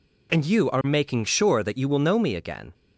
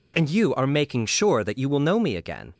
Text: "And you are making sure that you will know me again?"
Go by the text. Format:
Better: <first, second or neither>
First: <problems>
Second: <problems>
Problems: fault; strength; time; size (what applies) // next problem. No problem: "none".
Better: neither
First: none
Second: none